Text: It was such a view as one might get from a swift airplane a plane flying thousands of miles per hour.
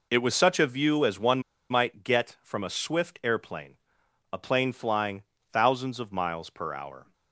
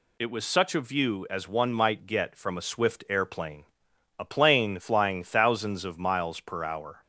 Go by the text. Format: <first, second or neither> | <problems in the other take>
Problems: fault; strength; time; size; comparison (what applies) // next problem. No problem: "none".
second | pauses between "one" and "might"; slight; at 1.4 s; 0.29 s long // pauses between "airplane" and "a"; noticeable; at 3.7 s; 0.56 s long; noticeable in the second // pauses between "flying" and "thousands"; slight; at 5.2 s; 0.30 s long